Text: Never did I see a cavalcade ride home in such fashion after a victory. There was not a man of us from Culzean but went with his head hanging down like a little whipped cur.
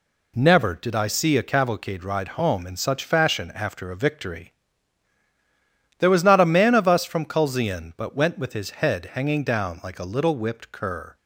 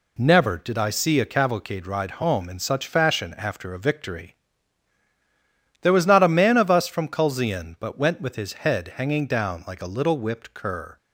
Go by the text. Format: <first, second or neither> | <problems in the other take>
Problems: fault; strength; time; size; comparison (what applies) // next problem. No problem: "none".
neither | none